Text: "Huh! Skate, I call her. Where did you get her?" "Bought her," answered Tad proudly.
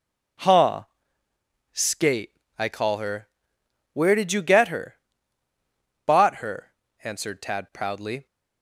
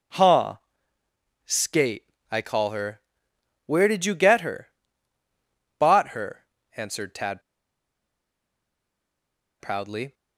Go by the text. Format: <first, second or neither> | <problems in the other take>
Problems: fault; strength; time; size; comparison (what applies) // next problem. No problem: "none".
first | pauses between "Tad" and "proudly"; strong; at 7.4 s; 2.1 s long